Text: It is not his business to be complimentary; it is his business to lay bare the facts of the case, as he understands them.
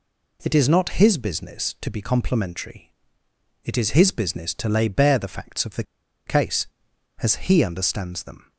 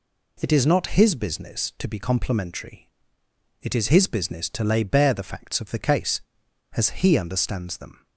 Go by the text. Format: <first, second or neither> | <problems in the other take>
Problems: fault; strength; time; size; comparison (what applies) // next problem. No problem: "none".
second | pauses between "the" and "case"; at 5.8 s; 0.43 s long